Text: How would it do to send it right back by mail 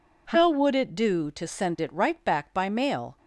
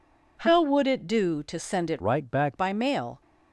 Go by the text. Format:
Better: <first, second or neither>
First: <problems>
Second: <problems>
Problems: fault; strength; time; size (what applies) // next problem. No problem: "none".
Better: first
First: none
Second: changes voice from "right" to "back"; from 2.0 to 2.5 s; 0.5 s long